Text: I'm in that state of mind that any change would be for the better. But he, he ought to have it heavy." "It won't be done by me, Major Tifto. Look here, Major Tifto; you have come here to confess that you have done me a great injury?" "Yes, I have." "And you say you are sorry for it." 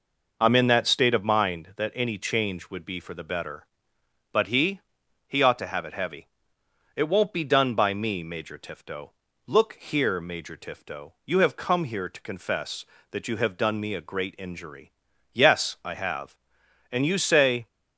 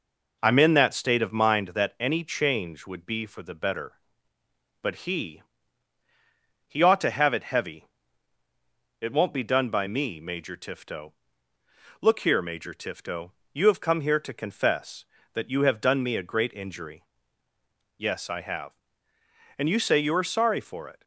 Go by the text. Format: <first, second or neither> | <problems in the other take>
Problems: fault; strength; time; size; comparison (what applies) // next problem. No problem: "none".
second | stops before "you are sorry for it"; at 17.6 s